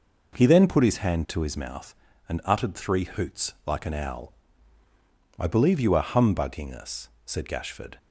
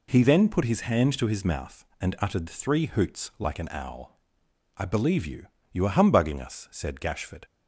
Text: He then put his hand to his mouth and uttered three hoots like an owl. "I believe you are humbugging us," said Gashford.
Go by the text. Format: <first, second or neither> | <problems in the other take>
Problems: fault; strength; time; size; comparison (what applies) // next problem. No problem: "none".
first | says "you" twice; at 5.7 s